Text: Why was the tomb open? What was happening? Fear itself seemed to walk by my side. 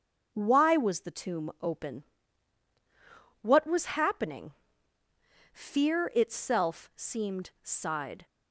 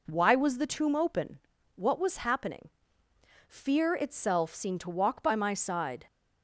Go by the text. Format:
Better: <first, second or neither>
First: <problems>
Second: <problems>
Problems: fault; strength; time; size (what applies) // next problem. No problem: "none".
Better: second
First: starts louder than the rest; until 1.3 s; 6 dB // skips "to walk by my"; at 7.5 s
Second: none